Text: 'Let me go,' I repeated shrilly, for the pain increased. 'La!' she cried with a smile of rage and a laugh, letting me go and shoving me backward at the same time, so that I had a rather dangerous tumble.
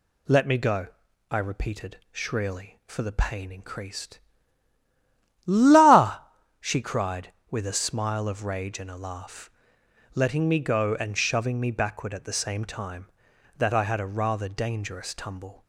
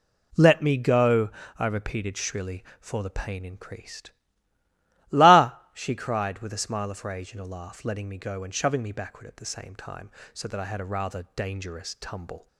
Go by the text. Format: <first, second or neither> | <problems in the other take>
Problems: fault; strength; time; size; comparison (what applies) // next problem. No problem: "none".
second | skips "so"; at 13.3 s